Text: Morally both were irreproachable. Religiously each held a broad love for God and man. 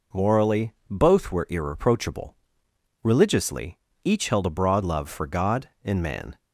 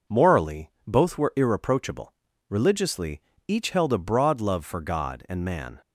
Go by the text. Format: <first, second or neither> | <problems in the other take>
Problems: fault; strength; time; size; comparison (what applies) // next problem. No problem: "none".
neither | pauses between "Morally" and "both"; slight; the same in both // pauses between "Religiously" and "each"; slight; the same in both